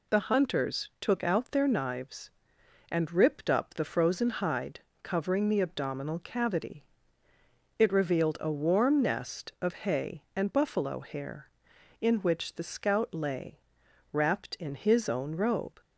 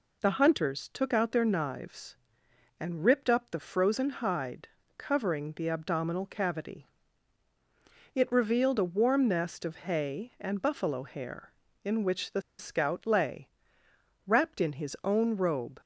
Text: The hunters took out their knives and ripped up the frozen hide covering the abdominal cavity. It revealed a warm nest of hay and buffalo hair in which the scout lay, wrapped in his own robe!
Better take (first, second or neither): first